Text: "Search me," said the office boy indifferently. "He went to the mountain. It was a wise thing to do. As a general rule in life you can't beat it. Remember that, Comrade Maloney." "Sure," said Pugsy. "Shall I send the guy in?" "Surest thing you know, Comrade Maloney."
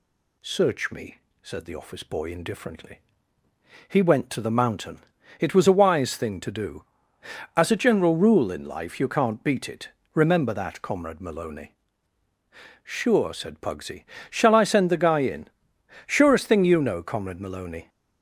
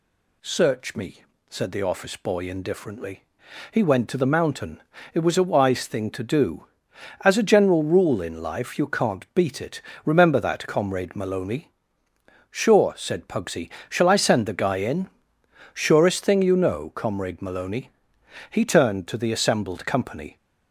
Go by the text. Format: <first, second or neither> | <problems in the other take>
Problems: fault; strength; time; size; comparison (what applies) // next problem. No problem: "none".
first | goes on to say "He turned to the assembled company"; strong; from 18.4 s on; 1.8 s long